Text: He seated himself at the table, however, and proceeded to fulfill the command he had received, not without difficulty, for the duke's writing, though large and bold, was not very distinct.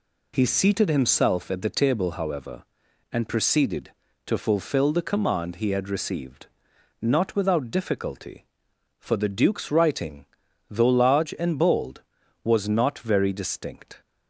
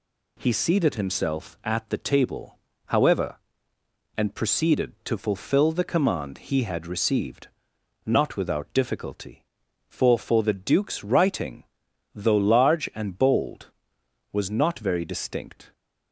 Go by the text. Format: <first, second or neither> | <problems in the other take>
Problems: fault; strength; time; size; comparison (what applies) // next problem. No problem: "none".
first | says "for" twice; at 10.1 s